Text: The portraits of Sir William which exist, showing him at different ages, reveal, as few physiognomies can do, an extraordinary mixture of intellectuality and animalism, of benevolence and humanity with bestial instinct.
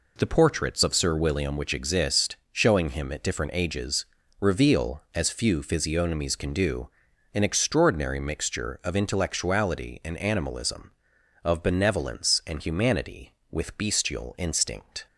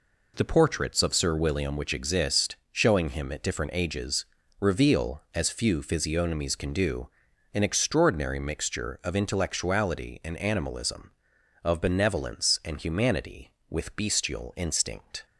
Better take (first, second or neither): neither